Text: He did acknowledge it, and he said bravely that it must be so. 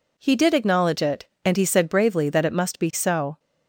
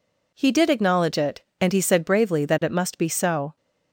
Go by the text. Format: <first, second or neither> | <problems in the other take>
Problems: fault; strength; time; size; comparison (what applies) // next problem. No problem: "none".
neither | none